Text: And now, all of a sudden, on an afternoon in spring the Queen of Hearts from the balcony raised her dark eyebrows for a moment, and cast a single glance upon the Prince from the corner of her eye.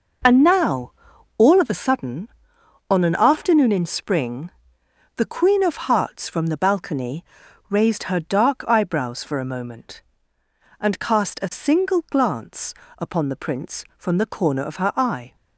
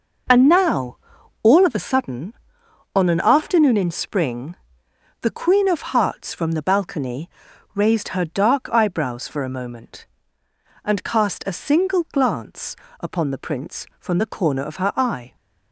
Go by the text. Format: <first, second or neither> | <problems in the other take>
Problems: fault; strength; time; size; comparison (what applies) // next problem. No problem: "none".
neither | pauses between "spring" and "the"; noticeable; the same in both // pauses between "balcony" and "raised"; noticeable; the same in both // pauses between "glance" and "upon"; slight; the same in both